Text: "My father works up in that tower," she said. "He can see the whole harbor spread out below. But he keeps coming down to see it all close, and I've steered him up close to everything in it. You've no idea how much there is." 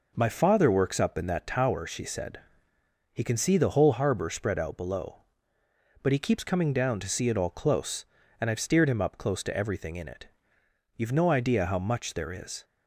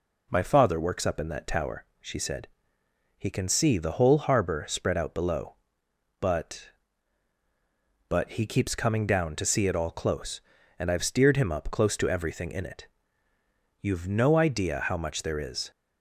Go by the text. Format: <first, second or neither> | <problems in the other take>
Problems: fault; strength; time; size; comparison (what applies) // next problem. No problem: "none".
first | says "But" twice; at 8.1 s